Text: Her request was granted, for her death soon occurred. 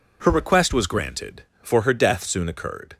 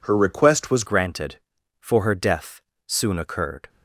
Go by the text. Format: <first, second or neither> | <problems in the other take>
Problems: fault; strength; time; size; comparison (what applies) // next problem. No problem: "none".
first | changes voice at "granted"; from 0.8 s on; 2.8 s long // pauses between "death" and "soon"; slight; at 2.6 s; 0.26 s long